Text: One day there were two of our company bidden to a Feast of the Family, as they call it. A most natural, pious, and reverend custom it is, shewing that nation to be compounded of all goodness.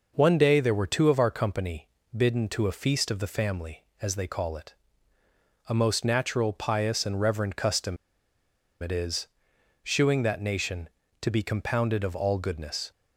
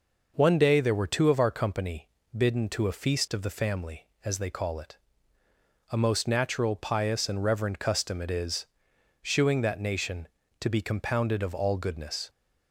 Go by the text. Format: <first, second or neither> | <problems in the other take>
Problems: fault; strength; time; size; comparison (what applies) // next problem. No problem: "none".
second | pauses between "company" and "bidden"; slight; at 1.8 s; 0.28 s long; slight in the second // pauses between "custom" and "it"; noticeable; at 7.9 s; 0.86 s long